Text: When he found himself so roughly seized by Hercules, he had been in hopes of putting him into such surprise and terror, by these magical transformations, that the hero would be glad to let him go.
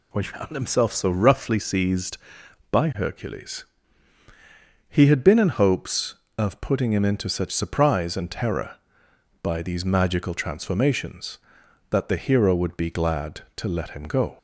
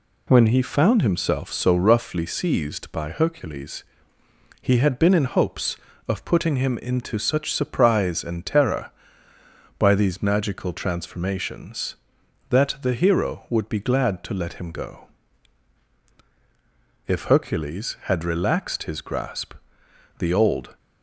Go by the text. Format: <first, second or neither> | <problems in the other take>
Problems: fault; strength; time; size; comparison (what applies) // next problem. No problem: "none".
first | goes on to say "If Hercules had relaxed his grasp the Old"; strong; from 17.0 s on; 3.7 s long